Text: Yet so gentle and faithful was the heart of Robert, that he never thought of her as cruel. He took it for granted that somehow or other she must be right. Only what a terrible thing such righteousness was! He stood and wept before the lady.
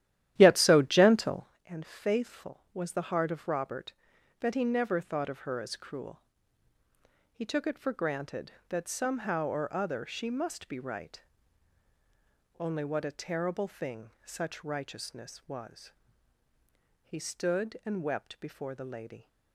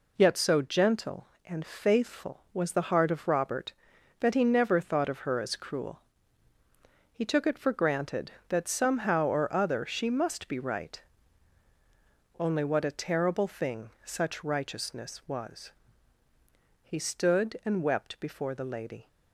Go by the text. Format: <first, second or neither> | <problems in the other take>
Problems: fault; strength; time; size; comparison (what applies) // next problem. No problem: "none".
second | starts louder than the rest; strong; until 1.6 s; 12.5 dB